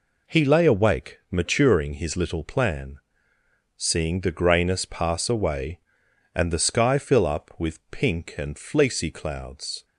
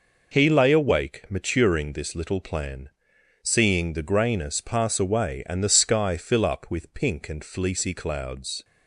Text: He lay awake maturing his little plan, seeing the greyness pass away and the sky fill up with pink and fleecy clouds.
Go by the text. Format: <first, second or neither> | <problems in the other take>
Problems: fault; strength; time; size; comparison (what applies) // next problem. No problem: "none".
first | says "this" for "his"; at 1.9 s